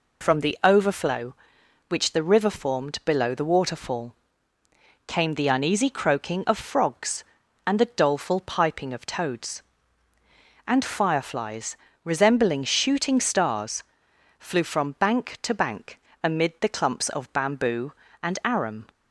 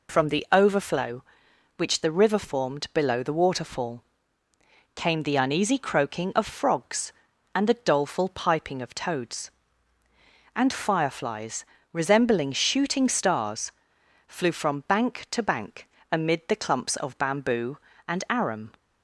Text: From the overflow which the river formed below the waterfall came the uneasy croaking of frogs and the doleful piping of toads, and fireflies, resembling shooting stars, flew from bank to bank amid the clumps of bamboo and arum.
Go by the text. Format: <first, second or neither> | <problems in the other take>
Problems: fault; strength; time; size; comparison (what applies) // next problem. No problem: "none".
neither | pauses between "waterfall" and "came"; noticeable; the same in both // pauses between "bank" and "amid"; slight; the same in both